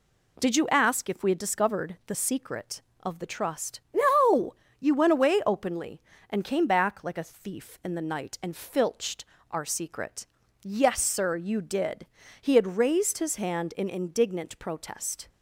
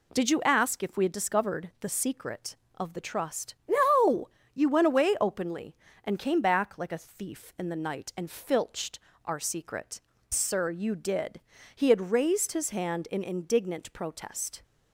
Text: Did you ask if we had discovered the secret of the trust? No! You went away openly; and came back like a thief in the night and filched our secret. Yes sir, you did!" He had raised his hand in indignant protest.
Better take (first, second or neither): first